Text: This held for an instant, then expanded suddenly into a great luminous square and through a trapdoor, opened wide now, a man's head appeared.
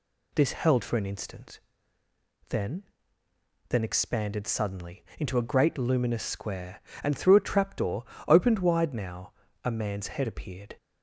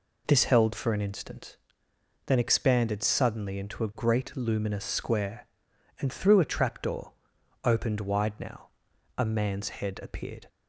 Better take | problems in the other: second | says "then" twice; at 3.6 s

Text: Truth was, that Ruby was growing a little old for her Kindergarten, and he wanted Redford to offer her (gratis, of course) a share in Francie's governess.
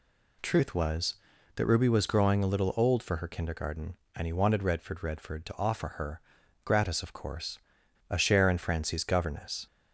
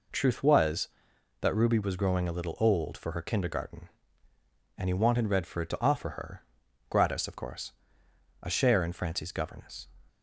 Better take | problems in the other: second | says "Redford" twice; at 5.0 s

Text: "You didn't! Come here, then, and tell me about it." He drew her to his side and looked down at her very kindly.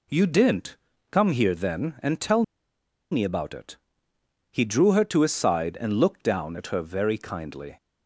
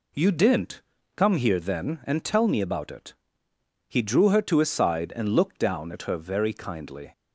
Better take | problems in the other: second | pauses between "tell" and "me"; noticeable; at 2.4 s; 0.69 s long

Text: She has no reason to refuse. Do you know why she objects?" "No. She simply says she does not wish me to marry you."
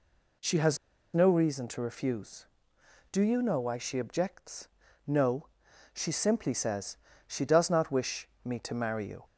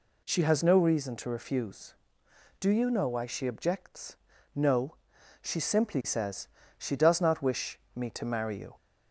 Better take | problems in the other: second | pauses between "has" and "no"; at 0.7 s; 0.37 s long // pauses between "says" and "she"; slight; at 6.9 s; 0.32 s long; slight in the second // pauses between "wish" and "me"; slight; at 8.2 s; 0.16 s long; slight in the second

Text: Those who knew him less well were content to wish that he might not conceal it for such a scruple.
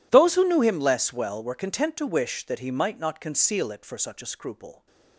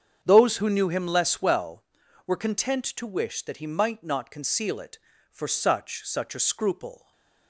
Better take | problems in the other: first | starts louder than the rest; strong; until 1.2 s; 7.5 dB // says "such" twice; at 6.0 s // stays silent after the last word; slight; from 6.9 s on; 0.5 s long

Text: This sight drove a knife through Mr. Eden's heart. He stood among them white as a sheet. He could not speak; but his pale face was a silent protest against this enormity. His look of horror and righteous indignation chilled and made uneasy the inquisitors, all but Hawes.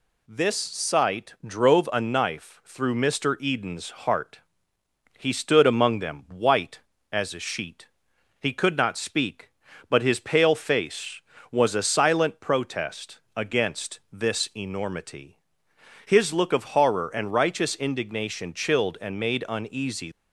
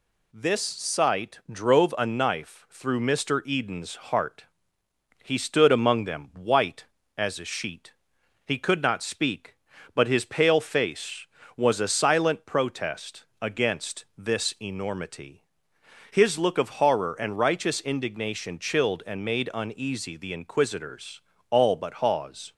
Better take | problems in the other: second | pauses between "protest" and "against"; slight; at 13.1 s; 0.16 s long; slight in the second // stops before "the inquisitors all but Hawes"; at 20.1 s

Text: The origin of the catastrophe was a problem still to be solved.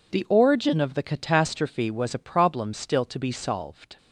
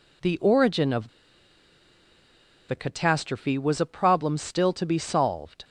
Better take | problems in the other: first | pauses between "of" and "the"; strong; at 1.0 s; 1.5 s long

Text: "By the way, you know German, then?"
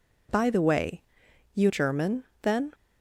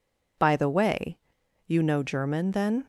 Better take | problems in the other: second | skips "know"; at 1.6 s

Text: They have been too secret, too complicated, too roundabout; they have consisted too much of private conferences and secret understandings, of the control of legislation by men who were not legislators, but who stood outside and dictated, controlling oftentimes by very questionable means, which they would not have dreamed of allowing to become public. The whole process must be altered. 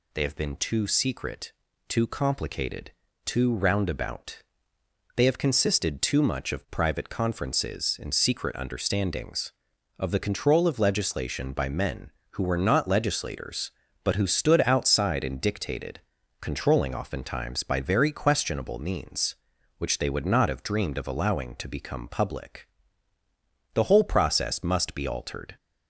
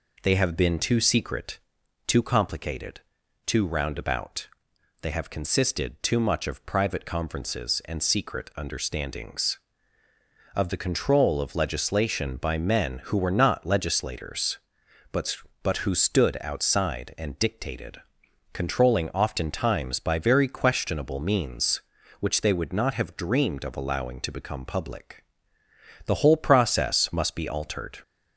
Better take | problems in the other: first | says "but" twice; at 15.6 s

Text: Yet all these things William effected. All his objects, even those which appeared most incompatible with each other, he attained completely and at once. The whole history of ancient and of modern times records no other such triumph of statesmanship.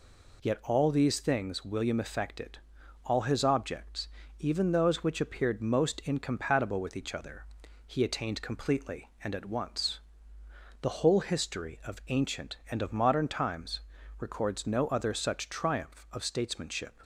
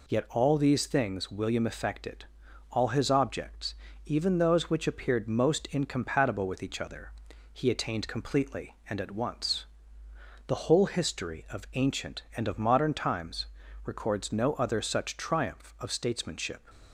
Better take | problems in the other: neither | pauses between "times" and "records"; the same in both

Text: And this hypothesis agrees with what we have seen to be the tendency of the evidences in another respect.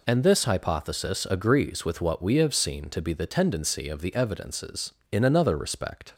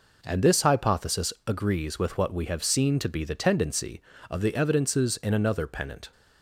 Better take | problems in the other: first | says "pennant" for "respect"; at 5.6 s

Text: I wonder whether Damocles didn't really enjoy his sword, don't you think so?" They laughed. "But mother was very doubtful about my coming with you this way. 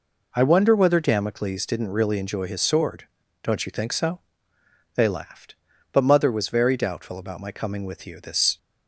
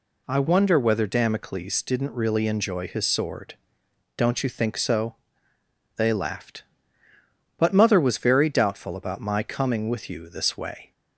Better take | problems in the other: second | stops before "way"; at 8.5 s

